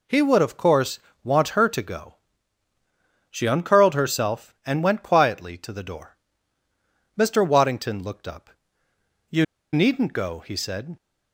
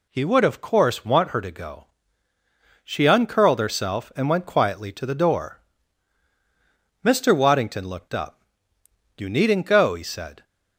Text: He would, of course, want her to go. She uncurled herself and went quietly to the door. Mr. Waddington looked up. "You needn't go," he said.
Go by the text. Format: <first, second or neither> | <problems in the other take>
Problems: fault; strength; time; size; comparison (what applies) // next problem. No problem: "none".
second | pauses between "You" and "needn't"; slight; at 9.4 s; 0.28 s long